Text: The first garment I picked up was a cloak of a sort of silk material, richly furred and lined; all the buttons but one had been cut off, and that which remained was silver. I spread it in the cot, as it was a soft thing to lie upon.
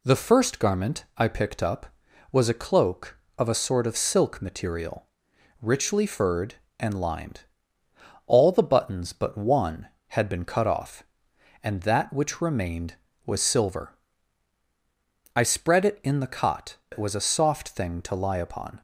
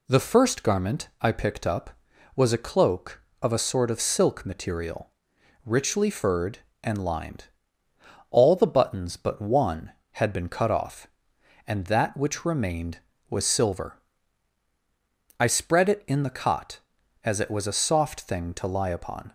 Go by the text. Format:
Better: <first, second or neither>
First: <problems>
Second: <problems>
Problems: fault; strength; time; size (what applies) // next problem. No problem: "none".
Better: second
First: skips "as"; at 16.8 s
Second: none